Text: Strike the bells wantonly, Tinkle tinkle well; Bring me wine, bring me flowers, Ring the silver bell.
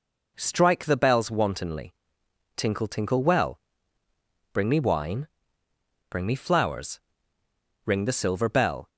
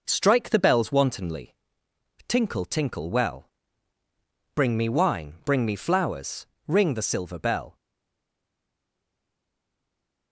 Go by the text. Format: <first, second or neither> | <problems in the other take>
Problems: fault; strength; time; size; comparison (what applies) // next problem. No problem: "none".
first | stays silent after the last word; strong; from 7.7 s on; 2.6 s long